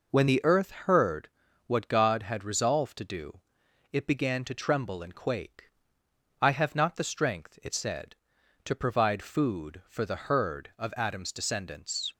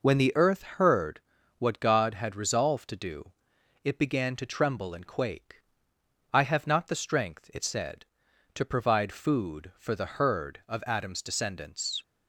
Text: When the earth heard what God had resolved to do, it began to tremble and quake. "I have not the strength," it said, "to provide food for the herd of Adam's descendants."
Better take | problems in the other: neither | pauses between "heard" and "what"; the same in both

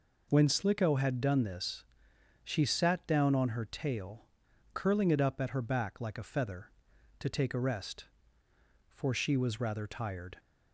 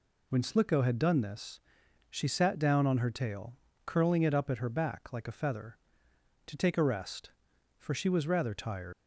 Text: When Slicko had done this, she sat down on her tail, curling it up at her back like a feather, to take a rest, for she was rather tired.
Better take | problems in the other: first | leaves "tired" unfinished; at 8.9 s; 135 ms

